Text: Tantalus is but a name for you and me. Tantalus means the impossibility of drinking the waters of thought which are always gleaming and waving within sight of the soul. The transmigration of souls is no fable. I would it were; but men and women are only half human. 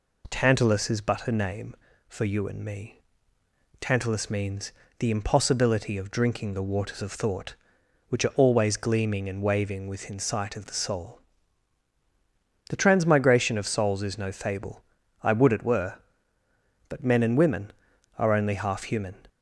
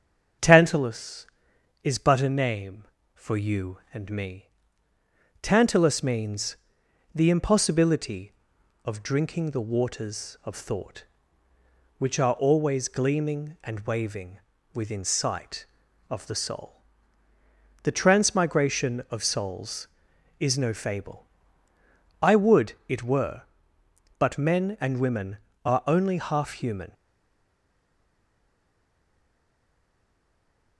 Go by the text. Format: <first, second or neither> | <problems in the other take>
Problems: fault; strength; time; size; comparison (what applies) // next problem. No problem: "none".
first | starts louder than the rest; strong; until 1.9 s; 7.5 dB // pauses between "means" and "the"; noticeable; at 6.5 s; 0.58 s long; slight in the first // pauses between "waving" and "within"; slight; at 14.3 s; 0.34 s long // stays silent after the last word; strong; from 26.9 s on; 3.8 s long